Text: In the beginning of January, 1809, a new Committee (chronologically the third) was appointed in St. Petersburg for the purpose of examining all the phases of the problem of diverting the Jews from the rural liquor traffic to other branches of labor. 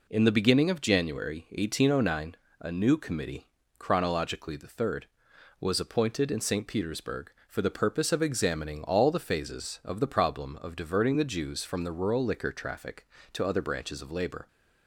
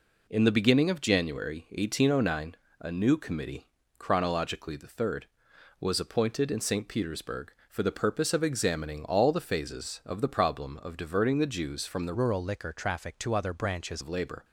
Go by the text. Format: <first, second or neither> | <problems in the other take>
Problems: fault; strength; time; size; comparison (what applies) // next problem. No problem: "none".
first | changes voice from "rural" to "branches"; from 12.1 to 14.0 s; 1.9 s long